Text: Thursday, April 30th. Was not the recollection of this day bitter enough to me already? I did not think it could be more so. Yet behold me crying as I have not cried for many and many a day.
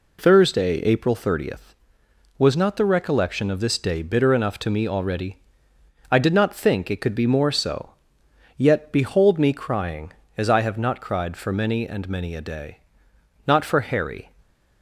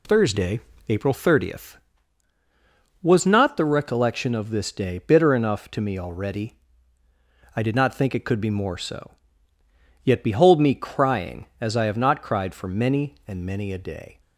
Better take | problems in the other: second | goes on to say "Not for Harry"; noticeable; from 13.4 s on; 0.84 s long

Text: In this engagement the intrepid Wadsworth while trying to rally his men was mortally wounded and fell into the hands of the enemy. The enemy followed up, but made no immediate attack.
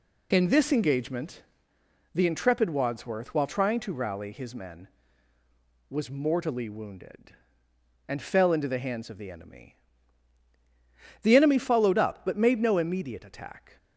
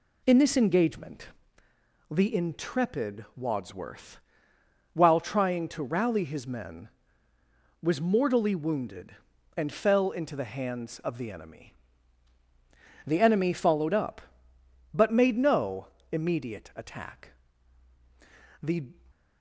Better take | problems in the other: first | pauses between "engagement" and "the"; noticeable; at 1.2 s; 0.80 s long; noticeable in the first // pauses between "Wadsworth" and "while"; noticeable; at 4.1 s; 0.74 s long // pauses between "no" and "immediate"; slight; at 15.8 s; 0.24 s long // goes on to say "The"; slight; from 18.6 s on; 0.30 s long

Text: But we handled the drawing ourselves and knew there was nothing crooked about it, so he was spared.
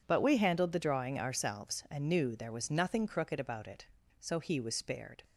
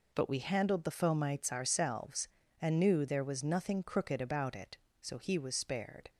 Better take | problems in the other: first | says "fomites" for "drawing"; at 0.9 s

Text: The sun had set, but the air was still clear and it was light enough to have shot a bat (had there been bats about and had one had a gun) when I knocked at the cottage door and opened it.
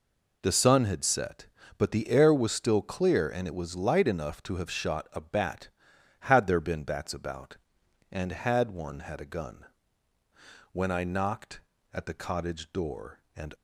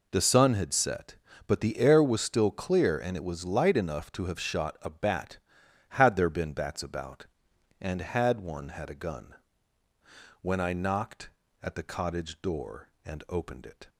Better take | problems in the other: second | stops before "opened it"; at 13.5 s

